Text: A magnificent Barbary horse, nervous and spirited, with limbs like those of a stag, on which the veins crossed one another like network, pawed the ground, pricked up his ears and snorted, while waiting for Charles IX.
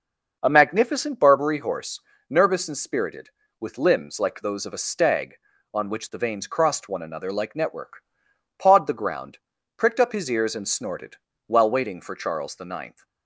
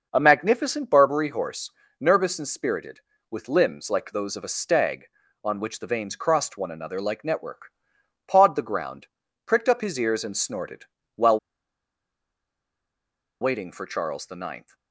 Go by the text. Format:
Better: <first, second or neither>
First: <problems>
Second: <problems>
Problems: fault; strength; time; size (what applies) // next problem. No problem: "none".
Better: first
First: starts louder than the rest; noticeable; until 1.4 s; 6 dB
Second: starts louder than the rest; noticeable; until 1.1 s; 6 dB // pauses between "while" and "waiting"; strong; at 11.3 s; 2.0 s long